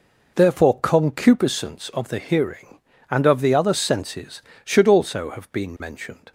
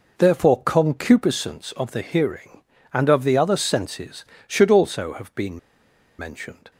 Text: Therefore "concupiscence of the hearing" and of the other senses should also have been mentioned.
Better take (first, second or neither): first